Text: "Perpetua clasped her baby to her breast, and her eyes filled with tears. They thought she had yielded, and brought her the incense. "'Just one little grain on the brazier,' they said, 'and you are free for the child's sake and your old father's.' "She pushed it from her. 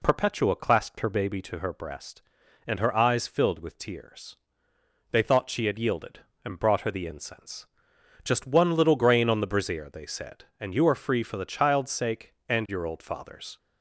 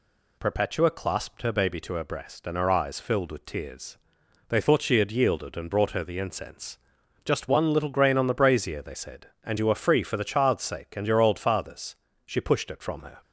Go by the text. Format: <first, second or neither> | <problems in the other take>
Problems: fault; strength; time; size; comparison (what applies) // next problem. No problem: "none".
second | stops before "She pushed it from her"; at 13.5 s